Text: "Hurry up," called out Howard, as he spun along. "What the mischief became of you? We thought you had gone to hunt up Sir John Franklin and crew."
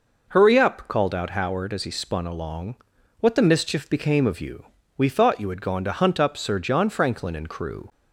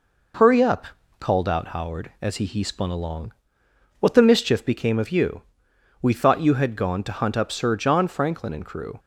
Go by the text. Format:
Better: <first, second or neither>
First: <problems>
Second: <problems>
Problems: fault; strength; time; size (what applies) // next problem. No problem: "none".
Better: first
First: none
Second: says "he" twice; at 2.4 s